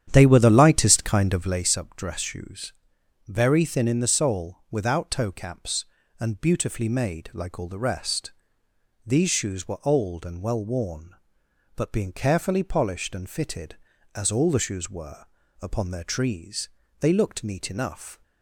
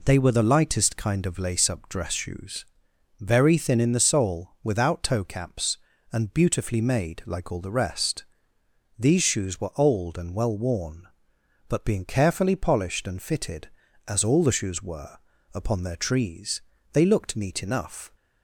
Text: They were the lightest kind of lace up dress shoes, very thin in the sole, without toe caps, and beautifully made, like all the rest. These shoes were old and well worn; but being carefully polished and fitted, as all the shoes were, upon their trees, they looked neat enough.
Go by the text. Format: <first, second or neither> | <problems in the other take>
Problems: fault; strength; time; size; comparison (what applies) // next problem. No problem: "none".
second | starts louder than the rest; strong; until 1.7 s; 9.5 dB